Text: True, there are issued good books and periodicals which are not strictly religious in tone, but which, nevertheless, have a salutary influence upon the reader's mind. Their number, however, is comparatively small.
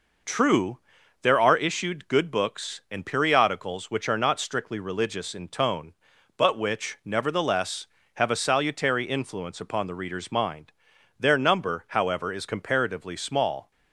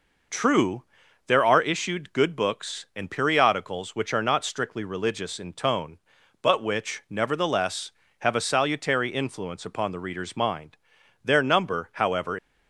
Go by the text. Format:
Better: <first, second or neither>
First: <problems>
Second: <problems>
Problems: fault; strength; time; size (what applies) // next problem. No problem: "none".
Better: first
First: none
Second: stops before "is comparatively small"; at 12.3 s